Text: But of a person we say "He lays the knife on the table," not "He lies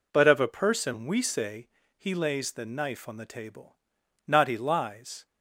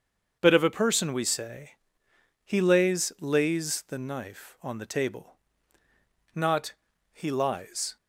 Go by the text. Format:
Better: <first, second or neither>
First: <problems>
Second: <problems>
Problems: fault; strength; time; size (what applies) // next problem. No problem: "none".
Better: first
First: pauses between "say" and "He"; slight; at 1.6 s; 0.28 s long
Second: starts louder than the rest; until 1.4 s; 7 dB // pauses between "say" and "He"; noticeable; at 1.7 s; 0.74 s long // says "lays" twice; at 3.1 s // pauses between "not" and "He"; at 6.7 s; 0.38 s long